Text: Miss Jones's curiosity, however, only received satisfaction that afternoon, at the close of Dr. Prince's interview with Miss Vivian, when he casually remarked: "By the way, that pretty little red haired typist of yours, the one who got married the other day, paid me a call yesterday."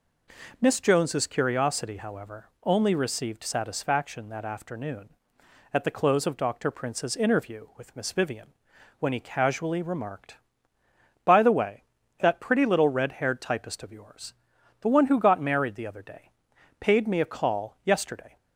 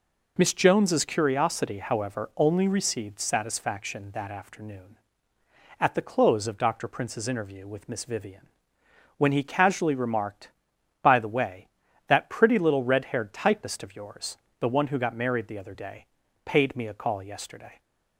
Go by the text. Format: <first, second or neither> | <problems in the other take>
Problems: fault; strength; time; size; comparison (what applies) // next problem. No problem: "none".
neither | none